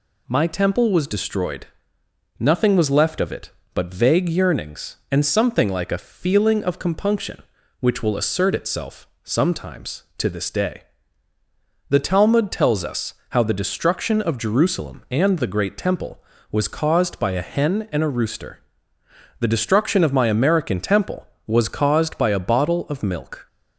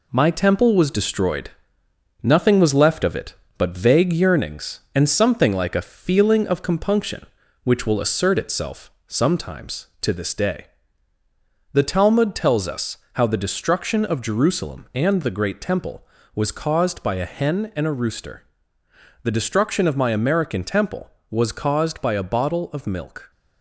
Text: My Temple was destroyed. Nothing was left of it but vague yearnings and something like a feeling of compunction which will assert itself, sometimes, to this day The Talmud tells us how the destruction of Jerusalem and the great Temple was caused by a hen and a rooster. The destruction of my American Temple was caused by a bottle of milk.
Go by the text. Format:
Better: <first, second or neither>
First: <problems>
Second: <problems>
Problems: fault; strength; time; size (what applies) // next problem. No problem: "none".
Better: first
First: pauses between "day" and "The"; at 10.8 s; 1.0 s long // pauses between "us" and "how"; slight; at 13.1 s; 0.18 s long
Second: gets quieter; noticeable; throughout; 5 dB // pauses between "day" and "The"; at 10.6 s; 1.0 s long // pauses between "us" and "how"; slight; at 12.9 s; 0.18 s long